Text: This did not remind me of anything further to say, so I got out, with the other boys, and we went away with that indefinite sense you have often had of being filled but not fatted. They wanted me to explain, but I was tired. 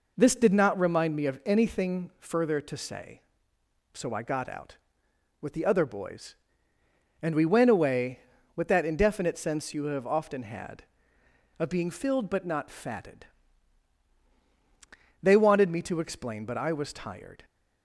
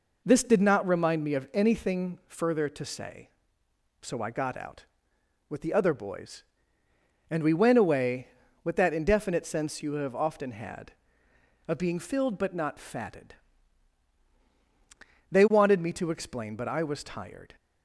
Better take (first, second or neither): neither